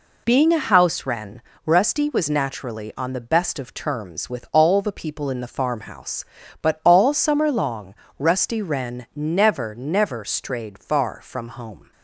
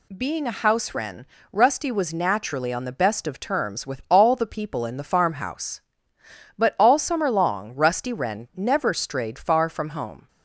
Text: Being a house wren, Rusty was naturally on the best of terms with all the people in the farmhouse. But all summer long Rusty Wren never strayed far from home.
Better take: second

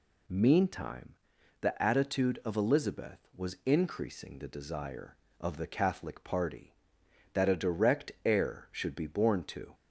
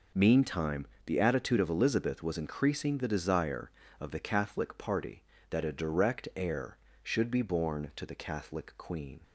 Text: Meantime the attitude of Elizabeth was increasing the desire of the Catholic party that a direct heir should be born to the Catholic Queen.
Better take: second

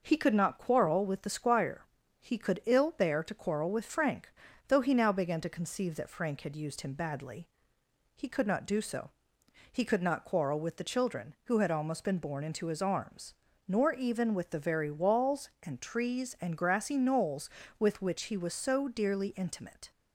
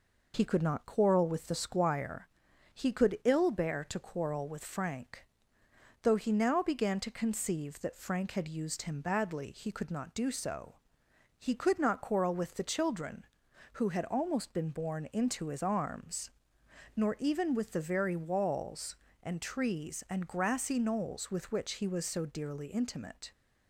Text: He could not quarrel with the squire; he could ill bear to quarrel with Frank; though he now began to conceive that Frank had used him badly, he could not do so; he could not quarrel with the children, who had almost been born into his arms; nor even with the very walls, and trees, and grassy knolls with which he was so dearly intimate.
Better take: neither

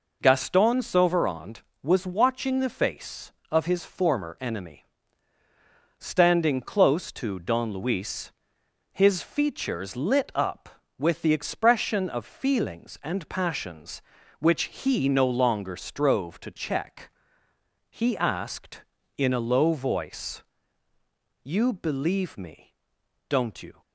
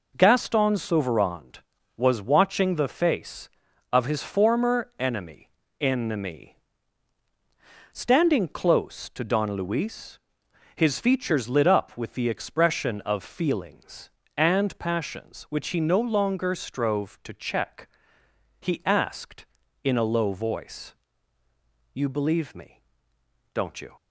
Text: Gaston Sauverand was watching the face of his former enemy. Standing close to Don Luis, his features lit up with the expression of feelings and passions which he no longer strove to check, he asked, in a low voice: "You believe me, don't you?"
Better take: first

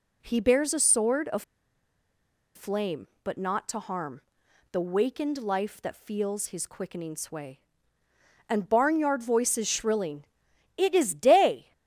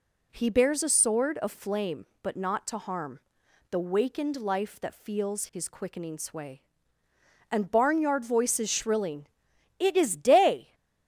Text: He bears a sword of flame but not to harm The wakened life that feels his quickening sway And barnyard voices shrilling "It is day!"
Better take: second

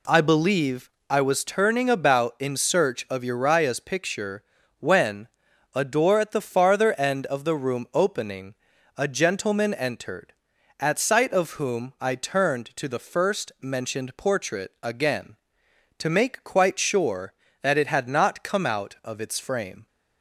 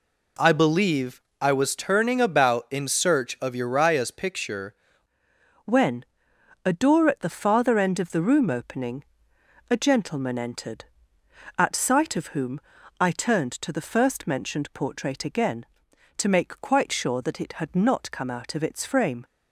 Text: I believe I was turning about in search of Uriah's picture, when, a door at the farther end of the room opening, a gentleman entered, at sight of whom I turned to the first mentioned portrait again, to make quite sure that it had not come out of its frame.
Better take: first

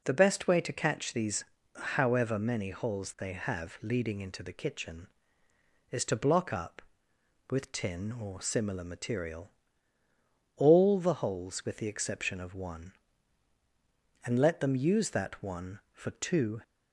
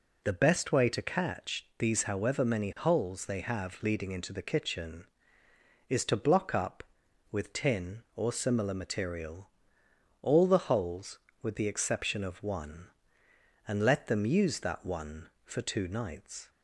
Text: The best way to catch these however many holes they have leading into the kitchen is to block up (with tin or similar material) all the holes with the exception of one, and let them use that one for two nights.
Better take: second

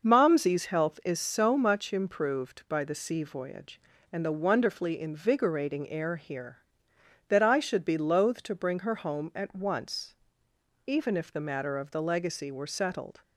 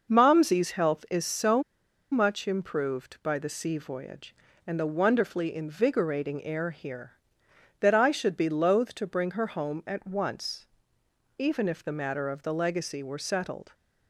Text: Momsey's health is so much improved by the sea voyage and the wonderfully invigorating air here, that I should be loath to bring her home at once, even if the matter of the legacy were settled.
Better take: first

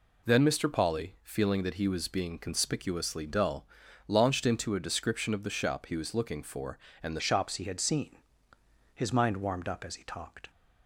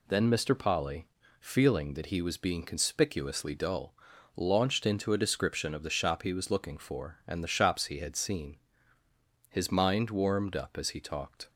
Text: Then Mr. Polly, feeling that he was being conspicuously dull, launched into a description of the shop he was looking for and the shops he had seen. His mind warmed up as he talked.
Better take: second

